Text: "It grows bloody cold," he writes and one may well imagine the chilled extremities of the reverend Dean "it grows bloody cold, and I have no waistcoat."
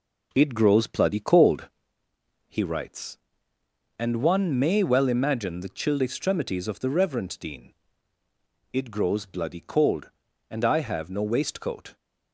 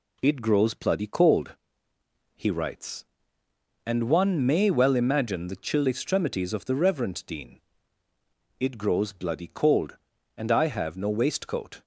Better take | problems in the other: second | starts louder than the rest; until 1.9 s; 3.5 dB // pauses between "Dean" and "it"; noticeable; at 7.7 s; 0.98 s long; noticeable in the second

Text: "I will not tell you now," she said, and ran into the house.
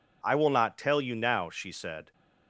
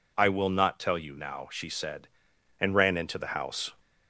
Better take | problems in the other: second | stops before "and ran into the house"; at 2.1 s

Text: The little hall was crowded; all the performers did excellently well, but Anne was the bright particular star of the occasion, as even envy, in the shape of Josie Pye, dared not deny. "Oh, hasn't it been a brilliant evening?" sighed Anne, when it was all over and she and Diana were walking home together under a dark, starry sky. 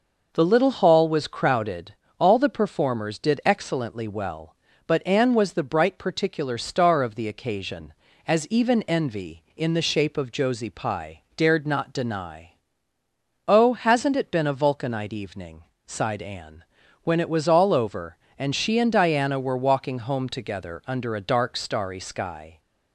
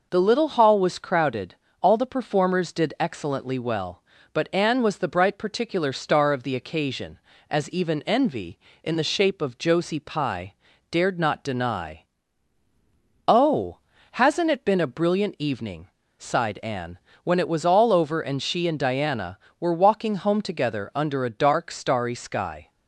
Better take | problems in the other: second | says "vulcanite" for "brilliant"; at 14.5 s

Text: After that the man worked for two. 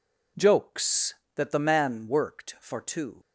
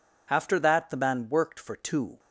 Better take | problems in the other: second | says "Jokes" for "After"; at 0.3 s

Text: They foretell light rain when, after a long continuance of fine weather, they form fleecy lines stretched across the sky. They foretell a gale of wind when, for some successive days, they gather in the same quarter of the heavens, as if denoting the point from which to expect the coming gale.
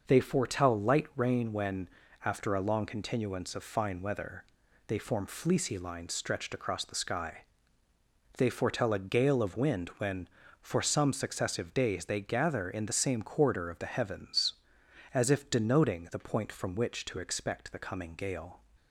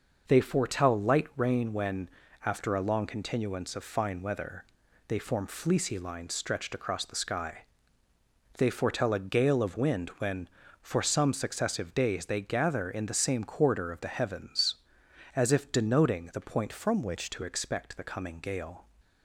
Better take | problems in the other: first | changes voice from "from" to "which"; from 16.7 to 17.2 s; 0.5 s long

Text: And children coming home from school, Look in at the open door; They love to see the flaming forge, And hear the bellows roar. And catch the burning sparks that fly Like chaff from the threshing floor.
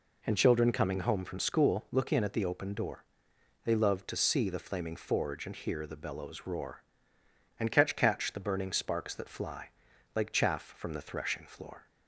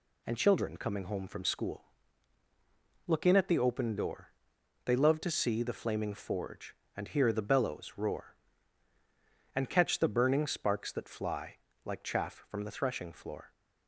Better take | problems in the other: second | says "catch" twice; at 7.9 s // pauses between "fly" and "Like"; at 9.7 s; 0.44 s long; slight in the second

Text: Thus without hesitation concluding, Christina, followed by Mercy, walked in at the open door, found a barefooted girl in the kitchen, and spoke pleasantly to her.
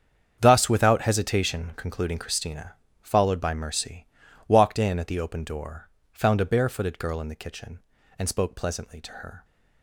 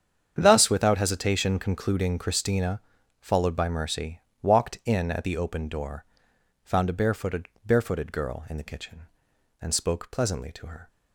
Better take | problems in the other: first | starts louder than the rest; strong; until 1.3 s; 8 dB; strong in the first // says "barefooted" twice; at 7.6 s

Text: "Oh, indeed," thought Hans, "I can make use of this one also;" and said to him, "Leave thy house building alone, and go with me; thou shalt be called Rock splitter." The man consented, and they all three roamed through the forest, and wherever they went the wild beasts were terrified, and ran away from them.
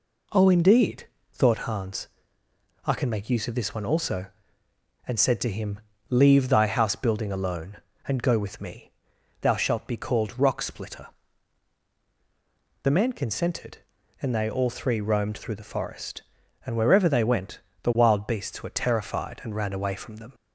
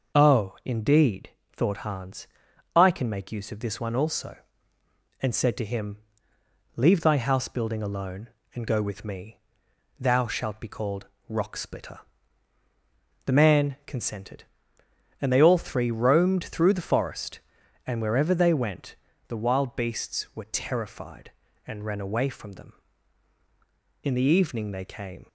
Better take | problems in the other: first | pauses between "called" and "Rock"; slight; at 11.0 s; 0.22 s long // pauses between "went" and "the"; slight; at 18.9 s; 0.32 s long; slight in the first // goes on to say "In the evening they came"; noticeable; from 24.0 s on; 1.2 s long

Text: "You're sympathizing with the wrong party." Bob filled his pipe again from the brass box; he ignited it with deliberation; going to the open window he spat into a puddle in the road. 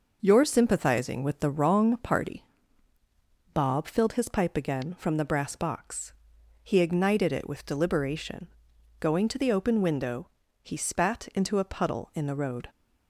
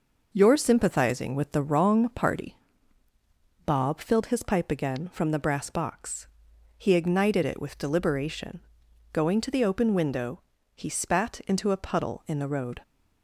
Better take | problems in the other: neither | pauses between "window" and "he"; slight; the same in both

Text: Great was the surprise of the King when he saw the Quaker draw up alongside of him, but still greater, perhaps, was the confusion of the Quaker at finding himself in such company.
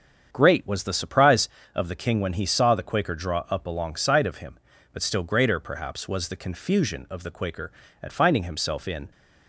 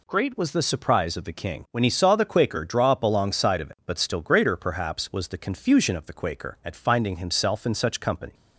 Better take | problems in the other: second | starts louder than the rest; strong; until 1.3 s; 7.5 dB // stops before "such company"; at 9.1 s

